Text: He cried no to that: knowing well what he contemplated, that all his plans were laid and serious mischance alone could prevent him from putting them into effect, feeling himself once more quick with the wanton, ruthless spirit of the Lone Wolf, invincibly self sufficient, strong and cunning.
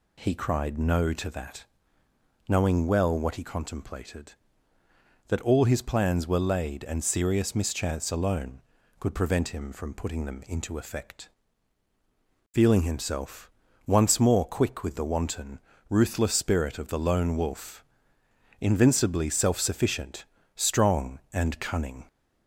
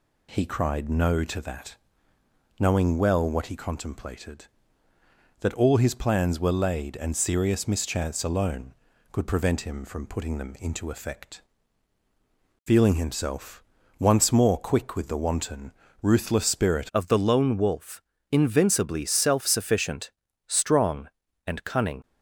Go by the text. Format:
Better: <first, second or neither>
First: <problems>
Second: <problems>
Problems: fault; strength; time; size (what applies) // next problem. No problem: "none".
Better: first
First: pauses between "himself" and "once"; slight; at 13.5 s; 0.34 s long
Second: pauses between "himself" and "once"; slight; at 13.6 s; 0.34 s long // changes voice at "of"; from 16.9 s on; 5.1 s long